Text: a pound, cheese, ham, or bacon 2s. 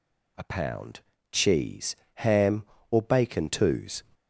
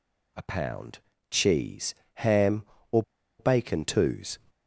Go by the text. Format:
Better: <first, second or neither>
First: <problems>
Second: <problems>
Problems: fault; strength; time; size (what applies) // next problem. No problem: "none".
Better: first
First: none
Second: pauses between "or" and "bacon"; at 3.0 s; 0.37 s long